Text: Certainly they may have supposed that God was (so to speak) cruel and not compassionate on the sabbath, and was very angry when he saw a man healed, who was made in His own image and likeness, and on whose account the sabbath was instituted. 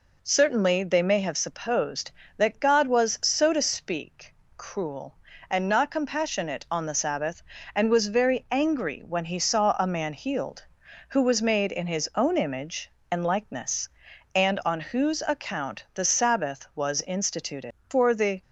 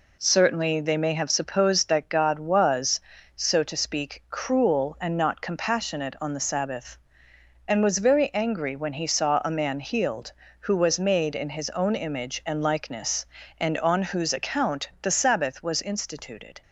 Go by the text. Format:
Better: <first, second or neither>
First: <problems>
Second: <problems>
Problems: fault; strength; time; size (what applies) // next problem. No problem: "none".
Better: second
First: goes on to say "For the"; from 17.8 s on; 0.54 s long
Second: none